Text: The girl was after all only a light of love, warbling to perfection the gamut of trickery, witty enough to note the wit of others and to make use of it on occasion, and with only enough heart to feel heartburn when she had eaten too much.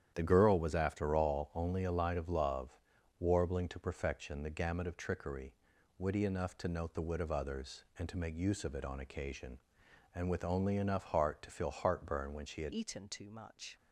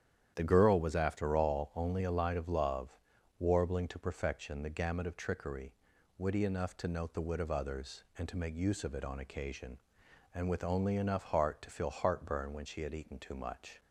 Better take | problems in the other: second | starts louder than the rest; strong; until 1.1 s; 9.5 dB; strong in the second // changes voice at "eaten"; from 12.7 s on; 1.0 s long

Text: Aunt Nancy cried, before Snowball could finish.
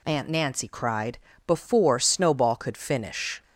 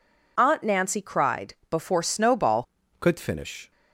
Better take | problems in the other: first | changes voice at "could"; from 3.0 s on; 0.7 s long

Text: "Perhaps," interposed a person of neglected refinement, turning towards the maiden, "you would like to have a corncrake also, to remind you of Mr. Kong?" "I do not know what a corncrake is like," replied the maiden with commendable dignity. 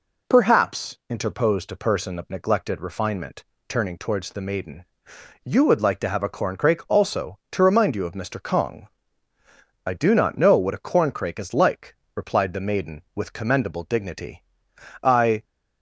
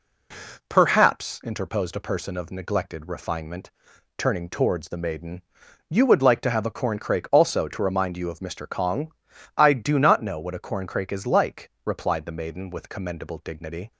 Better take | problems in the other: second | goes on to say "I"; slight; from 15.0 s on; 0.40 s long

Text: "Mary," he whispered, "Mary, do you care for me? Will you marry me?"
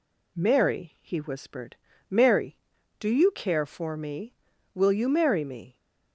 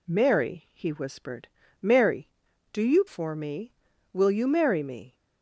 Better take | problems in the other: first | skips "care"; at 3.0 s

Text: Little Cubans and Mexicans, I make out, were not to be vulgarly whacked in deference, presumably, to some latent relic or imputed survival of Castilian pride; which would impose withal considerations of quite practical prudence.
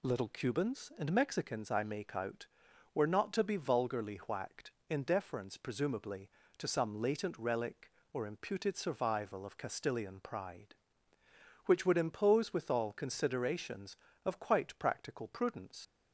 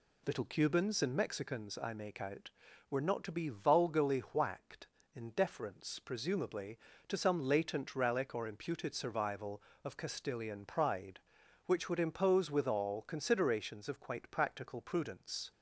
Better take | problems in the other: second | leaves "prudence" unfinished; at 15.8 s; 55 ms

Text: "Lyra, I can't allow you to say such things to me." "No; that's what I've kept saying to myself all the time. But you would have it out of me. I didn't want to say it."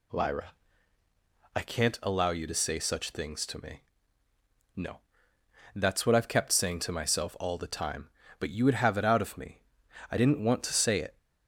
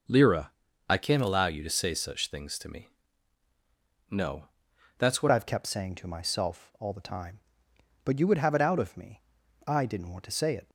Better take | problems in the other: first | changes voice at "I've"; from 5.3 s on; 5.3 s long

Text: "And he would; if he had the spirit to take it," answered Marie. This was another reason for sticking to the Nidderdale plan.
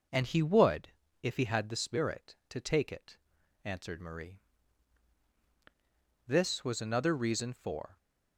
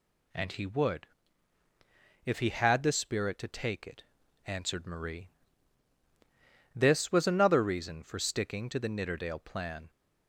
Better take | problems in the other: second | stops before "sticking to the Nidderdale plan"; at 7.9 s

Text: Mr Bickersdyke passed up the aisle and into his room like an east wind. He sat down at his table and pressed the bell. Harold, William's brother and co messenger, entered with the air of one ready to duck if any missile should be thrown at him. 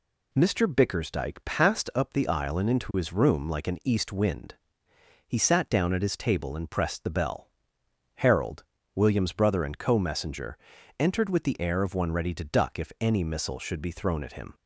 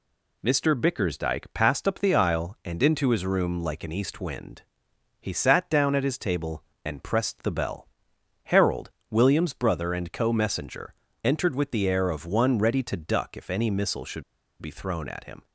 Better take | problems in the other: first | pauses between "should" and "be"; at 14.2 s; 0.38 s long

